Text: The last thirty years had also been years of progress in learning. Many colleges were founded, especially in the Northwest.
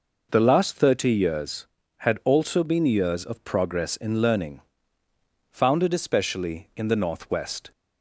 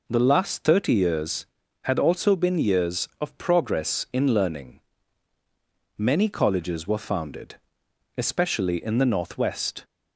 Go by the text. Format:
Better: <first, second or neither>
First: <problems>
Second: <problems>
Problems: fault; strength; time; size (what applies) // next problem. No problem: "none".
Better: second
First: skips "Many colleges were"; at 5.0 s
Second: none